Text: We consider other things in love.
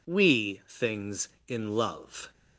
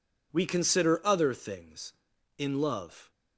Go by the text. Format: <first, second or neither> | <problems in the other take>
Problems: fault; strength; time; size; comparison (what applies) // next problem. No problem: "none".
second | skips "consider other"; at 0.6 s